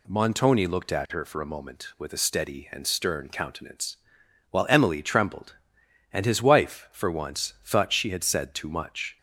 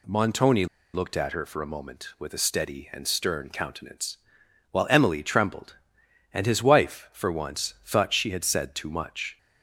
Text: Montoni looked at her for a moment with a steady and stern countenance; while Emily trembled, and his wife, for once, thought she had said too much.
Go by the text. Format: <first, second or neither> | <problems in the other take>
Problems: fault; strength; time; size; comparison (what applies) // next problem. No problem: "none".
first | pauses between "Montoni" and "looked"; slight; at 0.6 s; 0.28 s long